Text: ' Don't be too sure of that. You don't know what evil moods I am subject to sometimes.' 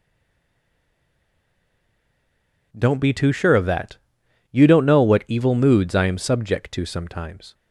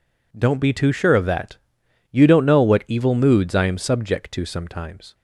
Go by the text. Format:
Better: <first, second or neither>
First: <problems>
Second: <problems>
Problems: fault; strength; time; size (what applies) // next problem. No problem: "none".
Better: second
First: stays silent before the first word; strong; until 2.7 s; 2.7 s long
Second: none